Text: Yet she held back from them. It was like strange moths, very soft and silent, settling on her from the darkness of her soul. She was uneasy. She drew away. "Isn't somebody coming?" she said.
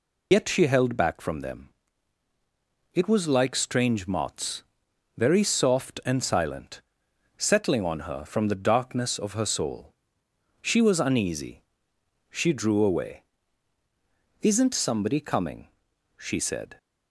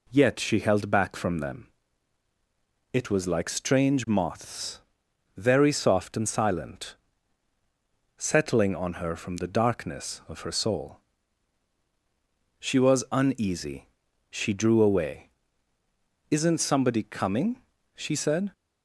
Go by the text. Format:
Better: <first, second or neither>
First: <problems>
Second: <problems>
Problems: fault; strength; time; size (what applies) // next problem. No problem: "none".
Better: second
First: loses the start of "Yet"; at 0.3 s; 85 ms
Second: none